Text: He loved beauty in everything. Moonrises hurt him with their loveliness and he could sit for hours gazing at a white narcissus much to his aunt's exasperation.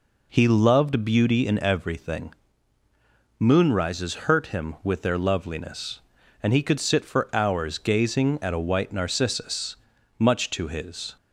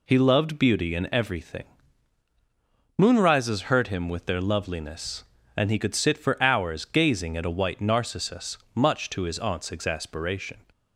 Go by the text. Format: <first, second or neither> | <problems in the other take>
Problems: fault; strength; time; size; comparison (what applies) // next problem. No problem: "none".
second | pauses between "narcissus" and "much"; noticeable; at 9.7 s; 0.46 s long; slight in the second // stops before "aunt's exasperation"; at 11.1 s